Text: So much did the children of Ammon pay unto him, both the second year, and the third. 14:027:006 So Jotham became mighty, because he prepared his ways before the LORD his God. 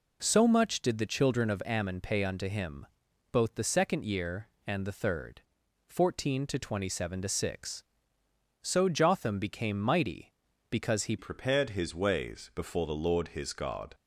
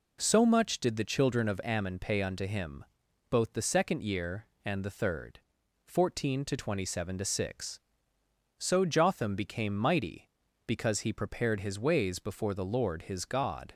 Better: second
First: changes voice at "prepared"; from 11.1 s on; 2.8 s long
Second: none

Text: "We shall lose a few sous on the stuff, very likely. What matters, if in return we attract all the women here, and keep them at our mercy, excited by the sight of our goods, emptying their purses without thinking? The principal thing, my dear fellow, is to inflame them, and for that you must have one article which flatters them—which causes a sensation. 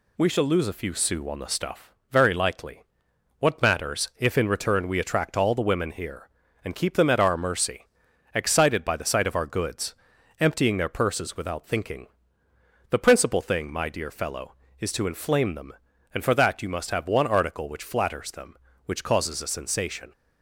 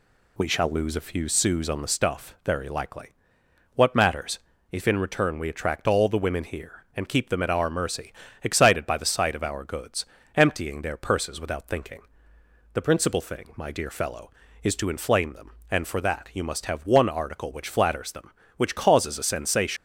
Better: first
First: none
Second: leaves "sensation" unfinished; at 19.7 s; 115 ms

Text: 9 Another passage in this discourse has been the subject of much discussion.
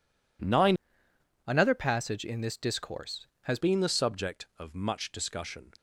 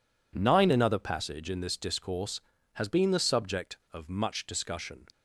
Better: second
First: changes voice from "Another" to "has"; from 1.4 to 3.5 s; 2.1 s long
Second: none

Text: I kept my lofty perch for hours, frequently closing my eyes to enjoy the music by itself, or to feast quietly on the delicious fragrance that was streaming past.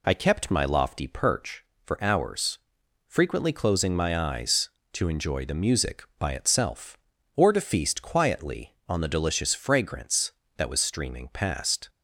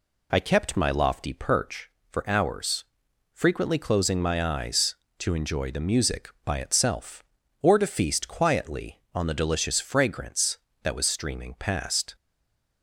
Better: first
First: none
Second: stays silent after the last word; slight; from 12.1 s on; 0.7 s long

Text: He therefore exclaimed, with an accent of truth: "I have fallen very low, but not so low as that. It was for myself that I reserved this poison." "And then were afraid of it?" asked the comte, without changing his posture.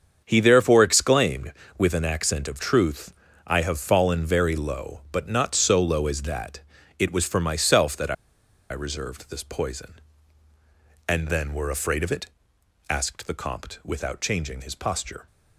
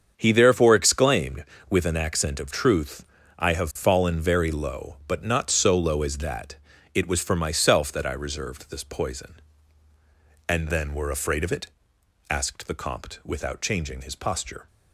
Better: second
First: starts louder than the rest; strong; until 1.2 s; 7 dB // pauses between "I" and "reserved"; noticeable; at 8.1 s; 0.57 s long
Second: starts louder than the rest; strong; until 1.1 s; 7 dB

